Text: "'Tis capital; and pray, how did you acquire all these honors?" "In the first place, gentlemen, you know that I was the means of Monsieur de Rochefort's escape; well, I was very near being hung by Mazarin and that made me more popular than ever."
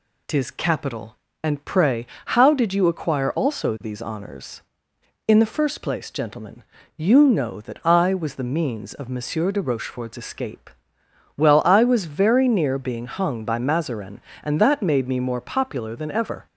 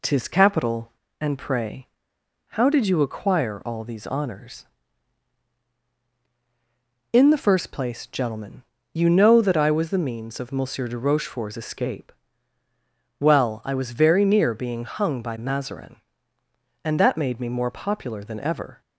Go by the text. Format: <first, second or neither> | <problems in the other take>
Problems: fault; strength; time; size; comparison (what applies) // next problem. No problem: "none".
second | says "also" for "all"; at 3.3 s